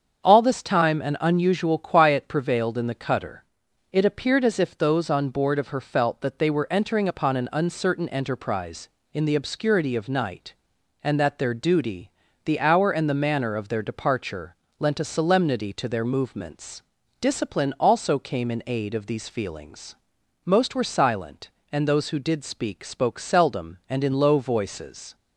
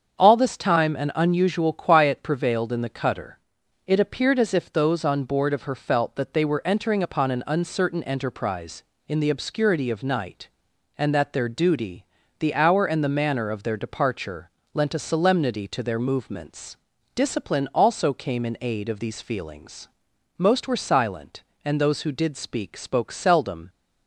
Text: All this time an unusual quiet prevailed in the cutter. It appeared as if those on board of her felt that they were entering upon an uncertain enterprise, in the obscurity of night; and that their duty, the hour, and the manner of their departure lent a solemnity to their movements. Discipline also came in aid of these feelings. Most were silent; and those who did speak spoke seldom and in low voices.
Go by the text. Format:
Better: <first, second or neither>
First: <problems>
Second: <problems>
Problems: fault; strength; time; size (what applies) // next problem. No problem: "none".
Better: first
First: starts louder than the rest; strong; until 1.2 s; 7.5 dB // pauses between "departure" and "lent"; slight; at 14.5 s; 0.24 s long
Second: starts louder than the rest; strong; until 1.2 s; 7.5 dB // pauses between "departure" and "lent"; slight; at 14.4 s; 0.24 s long // stops before "and in low voices"; at 23.6 s